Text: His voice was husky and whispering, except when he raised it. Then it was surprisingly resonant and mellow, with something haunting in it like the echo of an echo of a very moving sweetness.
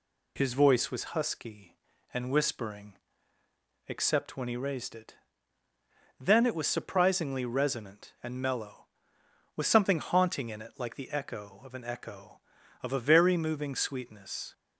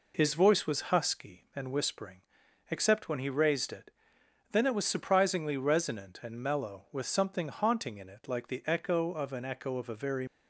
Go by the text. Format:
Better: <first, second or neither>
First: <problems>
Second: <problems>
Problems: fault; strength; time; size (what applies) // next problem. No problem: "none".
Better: first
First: none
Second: stops before "moving sweetness"; at 10.2 s